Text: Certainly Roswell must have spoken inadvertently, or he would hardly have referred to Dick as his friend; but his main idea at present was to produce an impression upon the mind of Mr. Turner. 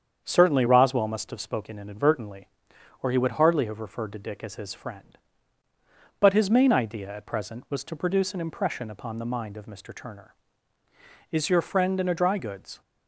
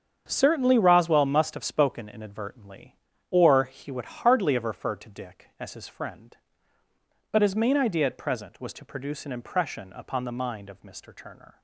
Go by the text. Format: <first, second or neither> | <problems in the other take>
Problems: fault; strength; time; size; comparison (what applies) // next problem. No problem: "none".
second | starts louder than the rest; strong; until 1.2 s; 7.5 dB; strong in the second // goes on to say "Is your friend in a dry goods"; from 11.3 s on; 1.4 s long